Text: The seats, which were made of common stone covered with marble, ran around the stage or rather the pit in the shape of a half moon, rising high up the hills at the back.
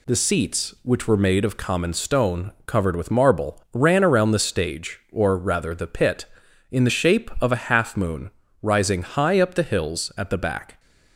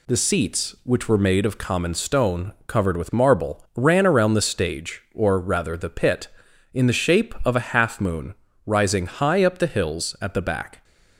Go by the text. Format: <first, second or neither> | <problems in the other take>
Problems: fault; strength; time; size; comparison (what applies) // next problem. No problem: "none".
neither | none